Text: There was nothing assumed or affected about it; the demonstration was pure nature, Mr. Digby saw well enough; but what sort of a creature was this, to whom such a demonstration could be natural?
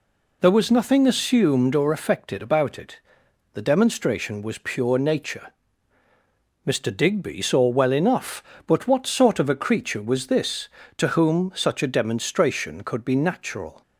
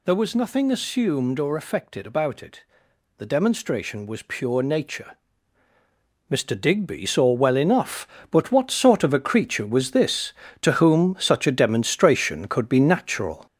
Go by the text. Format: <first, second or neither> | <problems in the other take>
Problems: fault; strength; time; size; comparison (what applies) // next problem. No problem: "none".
first | gets louder; noticeable; throughout; 5.5 dB